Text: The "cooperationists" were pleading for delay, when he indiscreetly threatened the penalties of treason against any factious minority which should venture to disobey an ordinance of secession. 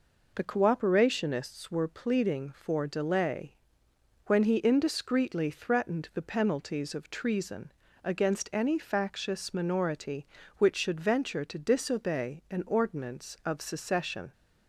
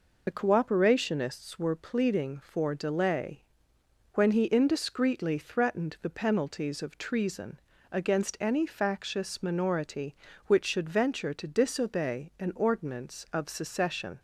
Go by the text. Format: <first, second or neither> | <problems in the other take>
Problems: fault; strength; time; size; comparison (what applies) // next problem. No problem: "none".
first | loses the start of "The"; at 0.2 s; 45 ms // pauses between "treason" and "against"; slight; at 7.6 s; 0.32 s long; slight in the first